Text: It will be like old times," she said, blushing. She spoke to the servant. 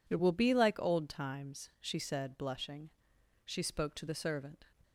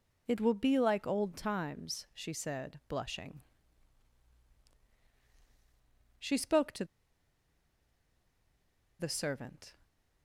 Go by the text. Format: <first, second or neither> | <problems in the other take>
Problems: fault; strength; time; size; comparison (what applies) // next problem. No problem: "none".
first | pauses between "to" and "the"; strong; at 6.8 s; 2.1 s long